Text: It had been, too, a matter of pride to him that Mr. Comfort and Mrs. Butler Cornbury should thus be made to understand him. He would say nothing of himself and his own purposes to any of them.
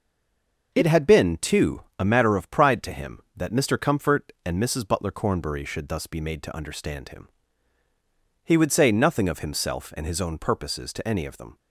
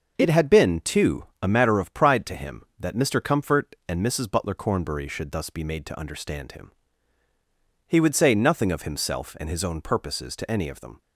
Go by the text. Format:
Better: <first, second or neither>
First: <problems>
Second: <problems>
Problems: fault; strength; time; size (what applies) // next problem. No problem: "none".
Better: second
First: stays silent before the first word; slight; until 0.7 s; 0.7 s long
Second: none